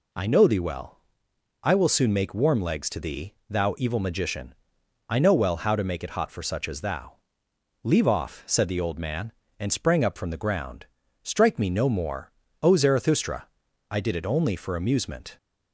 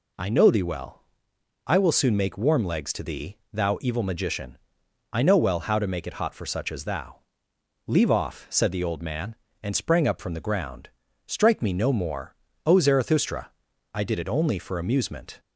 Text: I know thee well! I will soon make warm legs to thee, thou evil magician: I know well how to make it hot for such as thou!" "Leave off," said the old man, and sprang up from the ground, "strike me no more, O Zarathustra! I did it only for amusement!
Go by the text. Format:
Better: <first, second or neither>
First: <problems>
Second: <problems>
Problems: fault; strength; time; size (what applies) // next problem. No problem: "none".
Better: neither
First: none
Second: none